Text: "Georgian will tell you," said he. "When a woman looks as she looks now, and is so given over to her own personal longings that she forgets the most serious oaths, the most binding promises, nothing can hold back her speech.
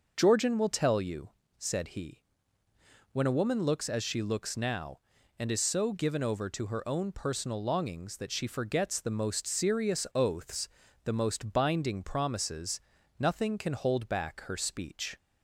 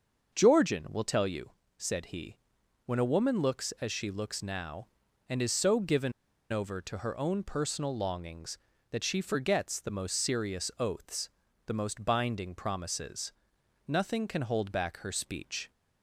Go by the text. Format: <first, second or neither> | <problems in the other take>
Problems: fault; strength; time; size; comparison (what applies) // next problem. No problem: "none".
first | starts louder than the rest; until 1.3 s; 6 dB // pauses between "given" and "over"; at 6.1 s; 0.40 s long